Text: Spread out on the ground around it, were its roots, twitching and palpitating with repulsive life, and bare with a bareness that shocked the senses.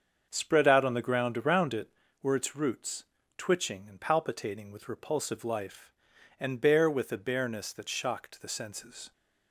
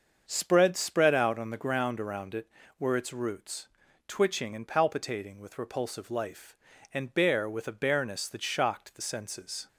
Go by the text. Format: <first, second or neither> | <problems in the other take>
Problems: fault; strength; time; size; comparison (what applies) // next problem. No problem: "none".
first | starts louder than the rest; until 1.2 s; 6.5 dB; also in the first // says "Spread" twice; at 0.7 s